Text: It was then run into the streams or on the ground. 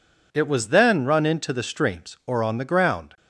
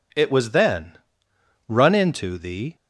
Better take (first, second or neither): first